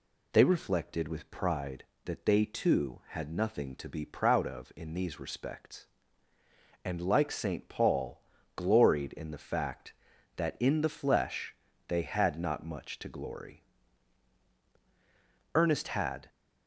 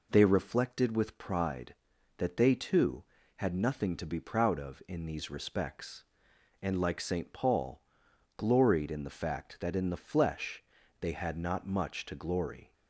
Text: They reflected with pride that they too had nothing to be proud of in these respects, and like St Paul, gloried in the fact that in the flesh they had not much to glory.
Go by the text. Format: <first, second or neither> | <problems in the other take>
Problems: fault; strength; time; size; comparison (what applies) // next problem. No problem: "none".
second | pauses between "flesh" and "they"; slight; at 11.5 s; 0.34 s long; also in the second // goes on to say "Ernest had"; noticeable; from 15.5 s on; 0.74 s long